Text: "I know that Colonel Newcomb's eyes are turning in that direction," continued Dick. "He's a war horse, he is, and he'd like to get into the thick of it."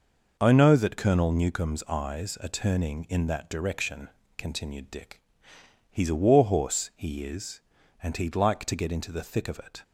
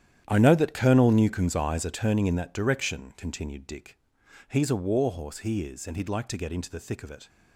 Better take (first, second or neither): first